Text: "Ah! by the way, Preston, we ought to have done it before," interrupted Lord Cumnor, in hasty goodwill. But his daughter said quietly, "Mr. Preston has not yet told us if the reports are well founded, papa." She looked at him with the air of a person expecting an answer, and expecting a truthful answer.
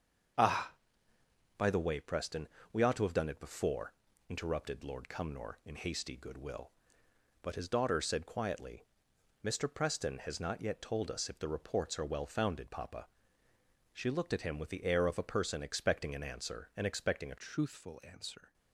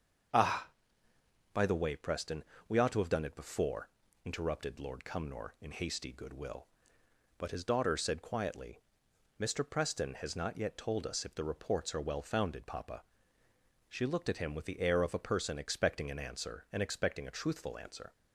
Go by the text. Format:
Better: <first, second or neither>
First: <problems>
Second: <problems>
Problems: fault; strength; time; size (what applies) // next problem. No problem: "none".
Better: second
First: starts louder than the rest; until 2.2 s; 7 dB // changes voice at "truthful"; from 17.3 s on; 1.2 s long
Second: starts louder than the rest; until 2.1 s; 7 dB